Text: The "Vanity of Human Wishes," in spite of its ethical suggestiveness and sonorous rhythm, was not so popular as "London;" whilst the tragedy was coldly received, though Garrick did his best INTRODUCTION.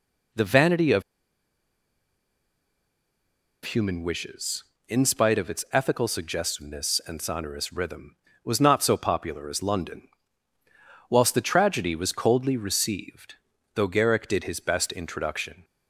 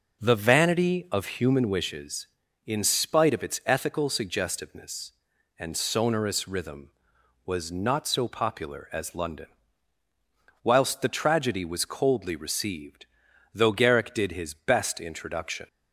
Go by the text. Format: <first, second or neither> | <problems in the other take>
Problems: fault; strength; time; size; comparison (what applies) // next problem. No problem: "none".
second | pauses between "of" and "Human"; strong; at 1.0 s; 2.6 s long